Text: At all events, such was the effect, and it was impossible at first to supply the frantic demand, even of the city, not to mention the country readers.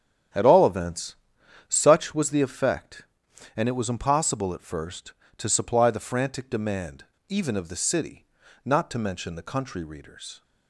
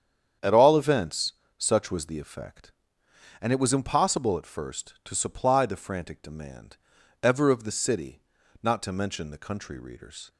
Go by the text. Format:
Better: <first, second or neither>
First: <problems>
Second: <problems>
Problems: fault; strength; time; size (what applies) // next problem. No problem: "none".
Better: first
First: starts louder than the rest; strong; until 1.8 s; 8.5 dB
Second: starts louder than the rest; strong; until 1.6 s; 8.5 dB // says "ever" for "even"; at 7.2 s